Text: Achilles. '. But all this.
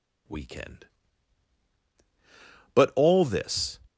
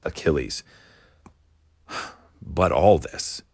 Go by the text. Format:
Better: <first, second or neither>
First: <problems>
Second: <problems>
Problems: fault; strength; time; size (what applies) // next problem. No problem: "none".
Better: second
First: says "Weekend" for "Achilles"; at 0.2 s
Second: none